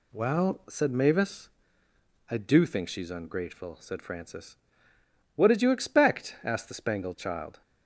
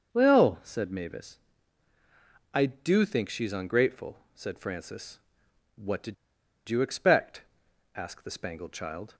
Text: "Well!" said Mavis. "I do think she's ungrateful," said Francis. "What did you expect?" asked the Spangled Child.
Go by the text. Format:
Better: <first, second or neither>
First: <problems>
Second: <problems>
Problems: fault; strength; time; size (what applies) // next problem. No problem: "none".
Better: first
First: none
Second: starts louder than the rest; noticeable; until 1.1 s; 6 dB // pauses between "did" and "you"; noticeable; at 6.1 s; 0.54 s long